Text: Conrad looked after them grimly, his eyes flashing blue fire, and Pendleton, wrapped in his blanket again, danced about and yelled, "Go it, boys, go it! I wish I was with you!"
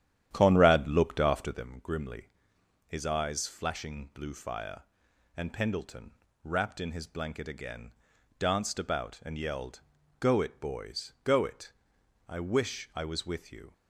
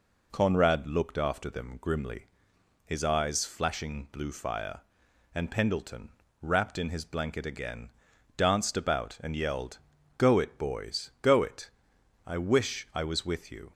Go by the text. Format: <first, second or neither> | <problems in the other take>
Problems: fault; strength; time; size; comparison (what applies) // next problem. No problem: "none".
second | starts louder than the rest; strong; until 1.6 s; 10.5 dB